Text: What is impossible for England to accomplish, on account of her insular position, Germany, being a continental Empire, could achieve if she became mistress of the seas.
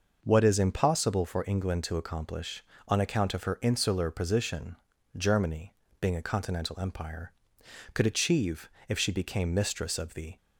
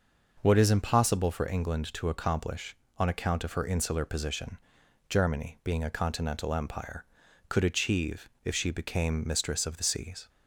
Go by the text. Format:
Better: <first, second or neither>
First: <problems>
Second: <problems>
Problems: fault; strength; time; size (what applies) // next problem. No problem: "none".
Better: second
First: pauses between "achieve" and "if"; slight; at 8.6 s; 0.18 s long // stops before "seas"; at 10.3 s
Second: pauses between "achieve" and "if"; slight; at 8.2 s; 0.16 s long